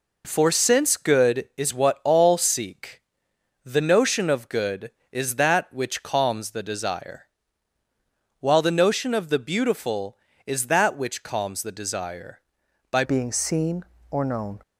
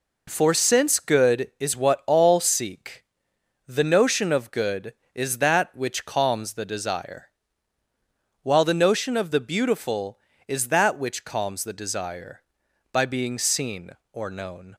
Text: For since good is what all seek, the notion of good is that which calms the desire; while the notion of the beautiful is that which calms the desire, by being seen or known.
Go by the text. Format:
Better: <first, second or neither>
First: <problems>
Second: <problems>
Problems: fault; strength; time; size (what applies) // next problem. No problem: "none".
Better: second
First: changes voice at "being"; from 13.0 s on; 1.6 s long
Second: none